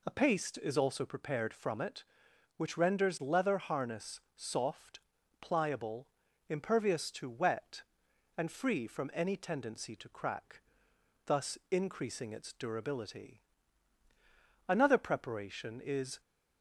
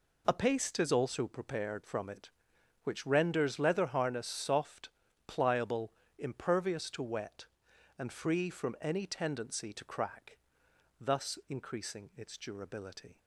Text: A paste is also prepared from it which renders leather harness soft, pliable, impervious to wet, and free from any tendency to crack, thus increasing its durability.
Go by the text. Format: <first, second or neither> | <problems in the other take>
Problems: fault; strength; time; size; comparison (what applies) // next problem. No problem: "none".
second | pauses between "harness" and "soft"; slight; at 4.1 s; 0.16 s long // goes on to say "Another preparation is"; from 14.6 s on; 1.5 s long